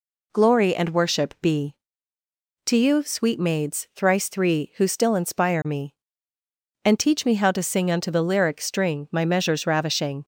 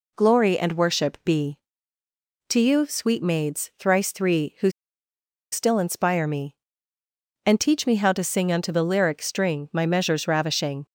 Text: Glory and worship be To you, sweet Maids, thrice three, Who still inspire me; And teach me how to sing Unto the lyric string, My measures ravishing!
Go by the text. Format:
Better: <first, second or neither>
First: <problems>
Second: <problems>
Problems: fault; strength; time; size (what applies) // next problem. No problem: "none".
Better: first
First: none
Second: pauses between "Who" and "still"; noticeable; at 4.6 s; 0.83 s long